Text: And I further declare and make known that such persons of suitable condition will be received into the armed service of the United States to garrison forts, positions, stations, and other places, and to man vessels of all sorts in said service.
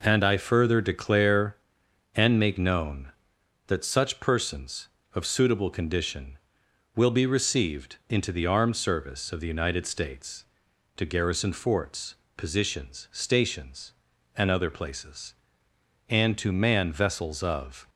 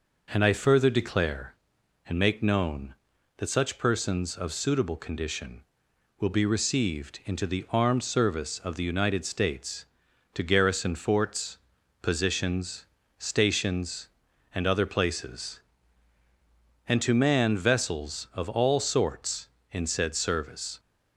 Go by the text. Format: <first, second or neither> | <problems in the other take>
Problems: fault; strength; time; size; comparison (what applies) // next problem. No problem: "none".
second | stops before "all sorts in said service"; at 17.8 s